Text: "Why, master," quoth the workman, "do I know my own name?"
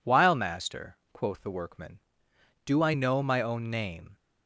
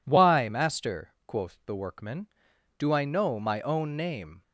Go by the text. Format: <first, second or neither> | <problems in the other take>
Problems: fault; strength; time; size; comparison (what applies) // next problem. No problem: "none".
second | says "While" for "Why"; at 0.0 s